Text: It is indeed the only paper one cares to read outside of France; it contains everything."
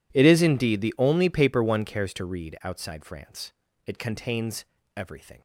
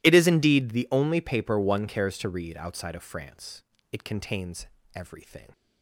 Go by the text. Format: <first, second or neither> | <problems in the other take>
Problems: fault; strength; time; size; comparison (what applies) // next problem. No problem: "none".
second | skips "of"; at 3.0 s // pauses between "contains" and "everything"; slight; at 4.6 s; 0.32 s long; slight in the second